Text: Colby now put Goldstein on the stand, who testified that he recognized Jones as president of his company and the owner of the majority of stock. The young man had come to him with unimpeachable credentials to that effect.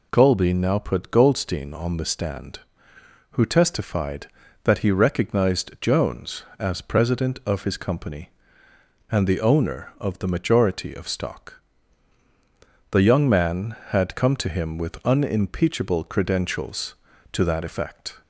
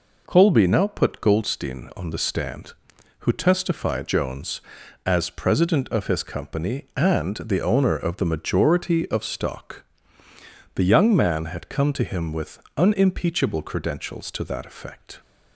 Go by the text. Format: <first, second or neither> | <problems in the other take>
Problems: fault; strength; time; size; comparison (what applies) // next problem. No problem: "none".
first | skips "that he recognized"; at 4.0 s // pauses between "with" and "unimpeachable"; slight; at 12.6 s; 0.16 s long